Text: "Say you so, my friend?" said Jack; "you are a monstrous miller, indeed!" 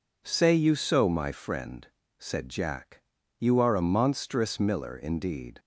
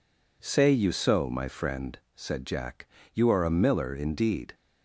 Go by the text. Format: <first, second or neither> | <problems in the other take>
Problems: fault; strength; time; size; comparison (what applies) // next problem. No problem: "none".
first | skips "monstrous"; at 3.5 s